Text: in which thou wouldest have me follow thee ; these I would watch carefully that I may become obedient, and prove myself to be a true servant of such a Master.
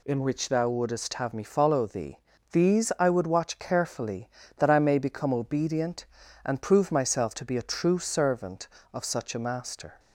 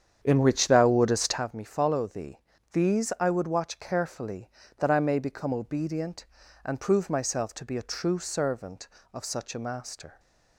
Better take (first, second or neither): first